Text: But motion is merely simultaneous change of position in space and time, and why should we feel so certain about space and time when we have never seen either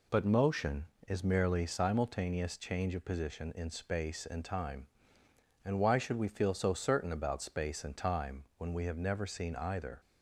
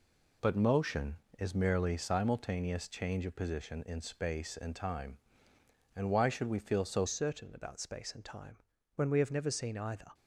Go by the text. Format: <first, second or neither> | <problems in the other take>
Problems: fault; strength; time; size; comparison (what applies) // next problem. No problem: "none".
first | changes voice at "certain"; from 7.0 s on; 3.1 s long // pauses between "time" and "when"; at 8.5 s; 0.38 s long